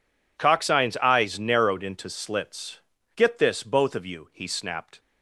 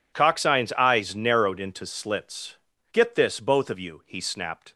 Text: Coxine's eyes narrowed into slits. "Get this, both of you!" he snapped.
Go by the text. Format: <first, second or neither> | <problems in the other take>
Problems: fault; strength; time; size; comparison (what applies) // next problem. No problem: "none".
neither | none